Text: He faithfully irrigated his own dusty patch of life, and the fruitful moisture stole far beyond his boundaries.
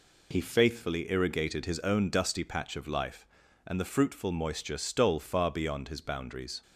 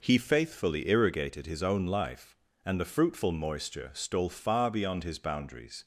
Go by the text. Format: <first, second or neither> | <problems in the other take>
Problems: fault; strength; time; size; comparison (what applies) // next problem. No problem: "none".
first | skips "dusty patch of"; at 1.8 s